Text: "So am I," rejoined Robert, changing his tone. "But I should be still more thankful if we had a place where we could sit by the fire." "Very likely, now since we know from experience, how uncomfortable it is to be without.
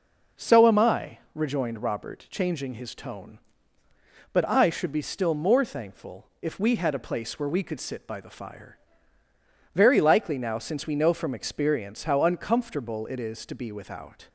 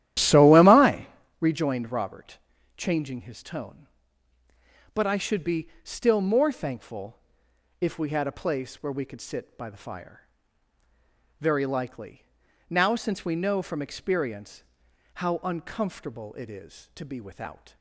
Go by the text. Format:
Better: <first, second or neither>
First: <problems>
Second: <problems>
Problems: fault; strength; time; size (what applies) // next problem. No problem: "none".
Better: first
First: none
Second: starts louder than the rest; strong; until 1.4 s; 12.5 dB // pauses between "be" and "still"; slight; at 5.6 s; 0.16 s long // pauses between "thankful" and "if"; noticeable; at 7.1 s; 0.60 s long